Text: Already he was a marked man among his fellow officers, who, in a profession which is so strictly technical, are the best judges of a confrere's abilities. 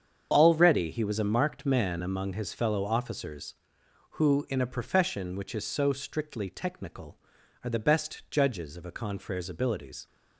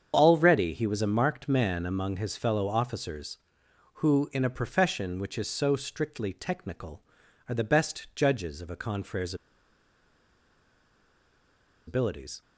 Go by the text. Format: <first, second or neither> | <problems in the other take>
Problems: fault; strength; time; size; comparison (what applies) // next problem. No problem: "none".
first | starts louder than the rest; strong; until 1.1 s; 7.5 dB; strong in the first // pauses between "confrere's" and "abilities"; strong; at 9.3 s; 2.5 s long